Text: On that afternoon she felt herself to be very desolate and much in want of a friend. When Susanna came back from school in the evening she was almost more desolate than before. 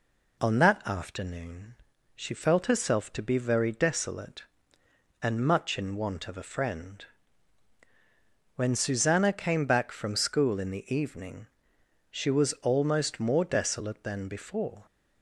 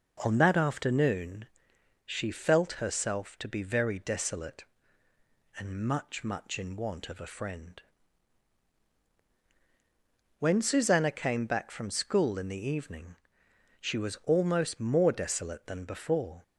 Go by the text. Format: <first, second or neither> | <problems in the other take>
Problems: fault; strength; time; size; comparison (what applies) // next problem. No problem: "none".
first | pauses between "afternoon" and "she"; noticeable; at 1.4 s; 0.58 s long; also in the first // says "much" twice; at 6.2 s // pauses between "evening" and "she"; noticeable; at 13.1 s; 0.66 s long; noticeable in the first